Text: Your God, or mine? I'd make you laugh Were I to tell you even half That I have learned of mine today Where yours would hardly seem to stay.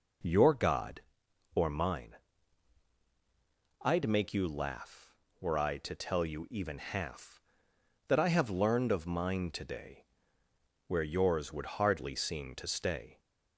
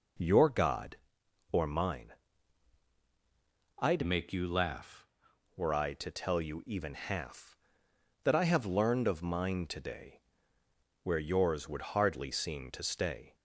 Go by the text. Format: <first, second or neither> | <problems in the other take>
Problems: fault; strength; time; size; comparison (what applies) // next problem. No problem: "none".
first | changes voice from "make" to "laugh"; from 4.0 to 5.0 s; 1.0 s long // pauses between "today" and "Where"; noticeable; at 10.1 s; 0.86 s long; noticeable in the first